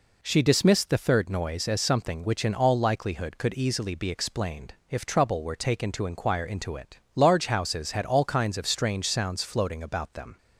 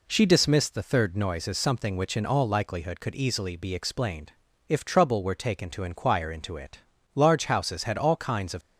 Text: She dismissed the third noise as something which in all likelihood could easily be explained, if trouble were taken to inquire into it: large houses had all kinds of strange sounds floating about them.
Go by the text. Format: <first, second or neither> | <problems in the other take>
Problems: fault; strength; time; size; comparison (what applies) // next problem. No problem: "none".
first | stops before "strange sounds floating about them"; at 8.6 s